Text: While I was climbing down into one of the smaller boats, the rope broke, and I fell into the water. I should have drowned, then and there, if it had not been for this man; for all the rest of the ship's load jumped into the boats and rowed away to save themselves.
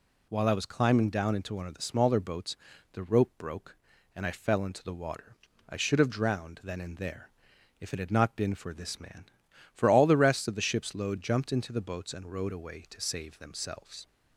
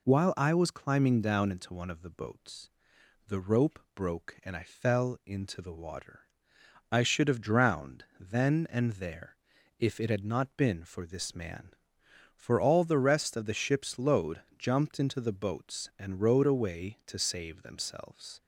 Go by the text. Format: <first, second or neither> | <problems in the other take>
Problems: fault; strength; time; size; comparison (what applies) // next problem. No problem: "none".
first | skips "smaller"; at 2.1 s // pauses between "rope" and "broke"; slight; at 3.7 s; 0.16 s long // pauses between "load" and "jumped"; slight; at 14.4 s; 0.18 s long